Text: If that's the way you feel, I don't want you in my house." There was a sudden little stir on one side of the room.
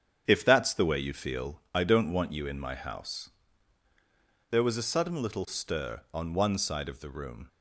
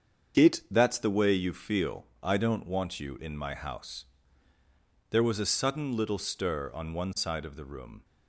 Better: first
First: starts louder than the rest; strong; until 1.2 s; 8 dB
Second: starts louder than the rest; strong; until 1.4 s; 7.5 dB // says "It" for "If"; at 0.3 s

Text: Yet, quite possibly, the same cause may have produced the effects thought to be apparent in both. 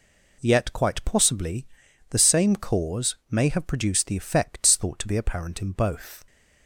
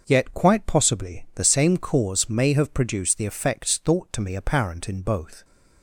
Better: first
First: none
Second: starts louder than the rest; until 1.0 s; 6.5 dB // says "me" for "be"; at 4.2 s

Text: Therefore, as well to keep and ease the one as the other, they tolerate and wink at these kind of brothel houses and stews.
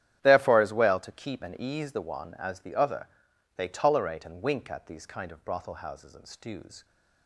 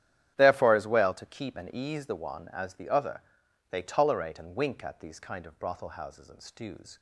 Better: neither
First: starts louder than the rest; strong; until 1.2 s; 11 dB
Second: starts louder than the rest; strong; until 1.3 s; 11 dB

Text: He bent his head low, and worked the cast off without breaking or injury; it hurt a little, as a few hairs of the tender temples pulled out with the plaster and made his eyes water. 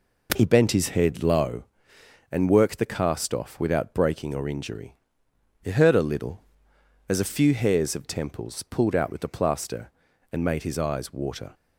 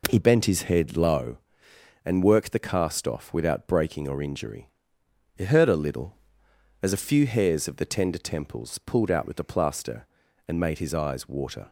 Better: second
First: skips "the tender"; at 8.0 s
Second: none

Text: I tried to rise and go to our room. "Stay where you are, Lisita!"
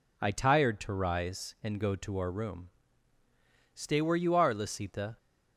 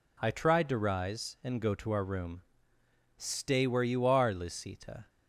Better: second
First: says "tired" for "tried"; at 0.3 s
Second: none

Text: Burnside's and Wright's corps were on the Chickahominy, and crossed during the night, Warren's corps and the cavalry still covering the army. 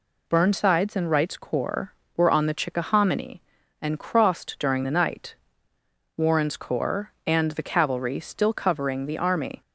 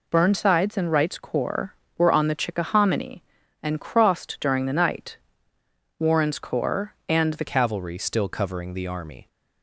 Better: first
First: none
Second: changes voice at "cavalry"; from 7.4 s on; 1.8 s long

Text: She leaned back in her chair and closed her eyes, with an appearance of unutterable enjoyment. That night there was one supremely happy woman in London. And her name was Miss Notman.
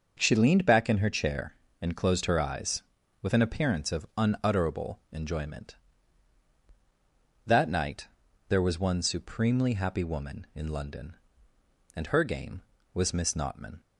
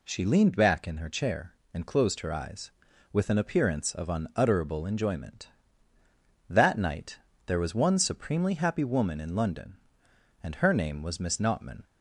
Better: second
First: starts louder than the rest; until 1.1 s; 6.5 dB // pauses between "night" and "there"; at 8.0 s; 0.40 s long // says "game" for "name"; at 12.2 s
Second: pauses between "night" and "there"; slight; at 7.1 s; 0.28 s long

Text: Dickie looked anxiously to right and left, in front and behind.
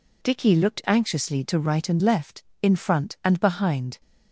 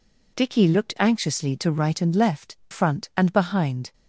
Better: first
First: none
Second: skips "in"; at 2.6 s

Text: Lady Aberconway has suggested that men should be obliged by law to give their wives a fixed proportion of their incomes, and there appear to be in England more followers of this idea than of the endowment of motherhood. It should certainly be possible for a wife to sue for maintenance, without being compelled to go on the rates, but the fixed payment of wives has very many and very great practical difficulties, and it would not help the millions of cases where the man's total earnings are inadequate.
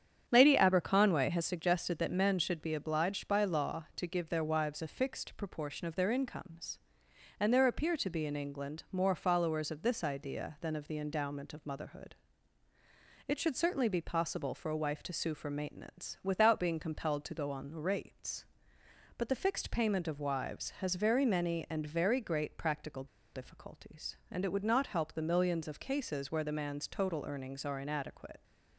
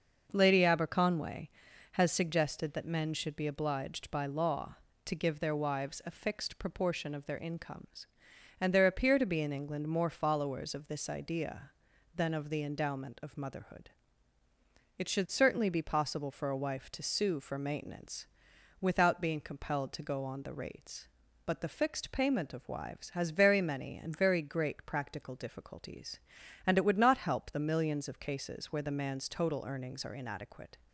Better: second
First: starts louder than the rest; strong; until 1.2 s; 8.5 dB // pauses between "practical" and "difficulties"; slight; at 23.0 s; 0.28 s long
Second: starts louder than the rest; noticeable; until 1.3 s; 6 dB

